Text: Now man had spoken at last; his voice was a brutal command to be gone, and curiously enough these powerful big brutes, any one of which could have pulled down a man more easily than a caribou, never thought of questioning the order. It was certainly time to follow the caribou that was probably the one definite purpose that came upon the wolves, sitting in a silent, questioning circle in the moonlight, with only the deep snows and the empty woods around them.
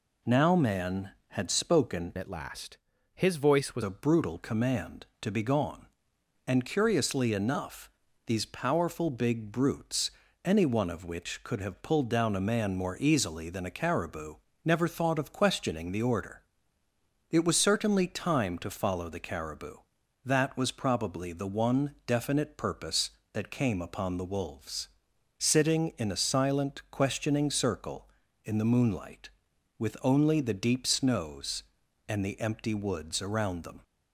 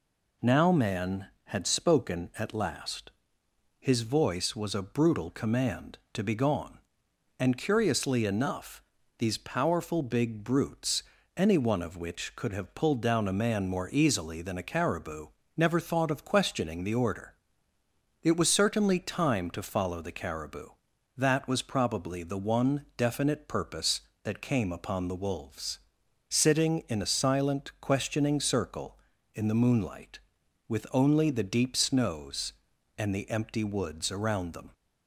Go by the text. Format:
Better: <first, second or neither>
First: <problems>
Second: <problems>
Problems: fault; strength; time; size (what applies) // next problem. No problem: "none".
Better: second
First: changes voice from "at" to "was"; from 2.1 to 3.8 s; 1.7 s long // pauses between "enough" and "these"; slight; at 7.9 s; 0.34 s long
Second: pauses between "enough" and "these"; slight; at 8.8 s; 0.34 s long